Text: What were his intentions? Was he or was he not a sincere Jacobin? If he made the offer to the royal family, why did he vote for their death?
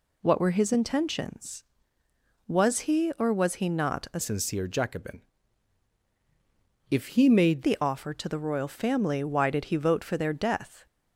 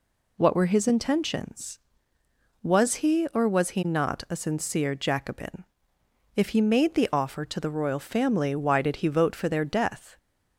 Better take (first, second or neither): second